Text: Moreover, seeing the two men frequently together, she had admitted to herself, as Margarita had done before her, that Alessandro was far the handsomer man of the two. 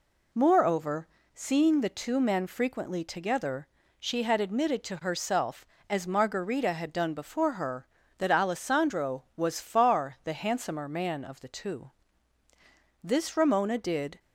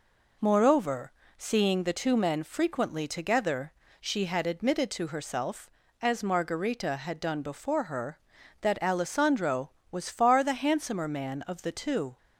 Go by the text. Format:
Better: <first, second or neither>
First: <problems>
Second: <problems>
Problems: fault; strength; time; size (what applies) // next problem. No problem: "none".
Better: second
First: goes on to say "This Ramona did"; noticeable; from 13.0 s on; 1.1 s long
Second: none